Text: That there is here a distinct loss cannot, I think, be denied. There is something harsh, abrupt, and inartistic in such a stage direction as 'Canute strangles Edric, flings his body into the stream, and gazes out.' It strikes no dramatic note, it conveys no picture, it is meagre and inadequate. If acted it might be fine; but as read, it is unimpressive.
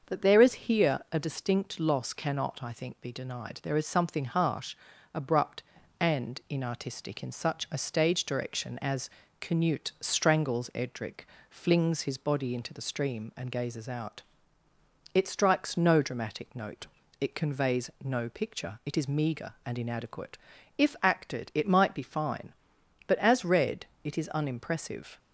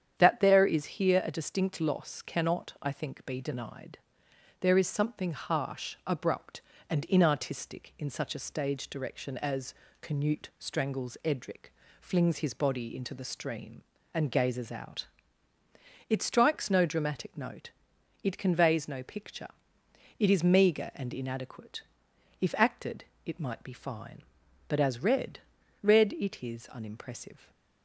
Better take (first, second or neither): first